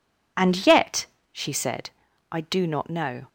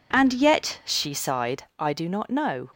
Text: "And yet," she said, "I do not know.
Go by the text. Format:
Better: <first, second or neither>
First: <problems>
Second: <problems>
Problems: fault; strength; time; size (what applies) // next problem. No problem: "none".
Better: first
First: none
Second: says "sighed" for "said"; at 1.1 s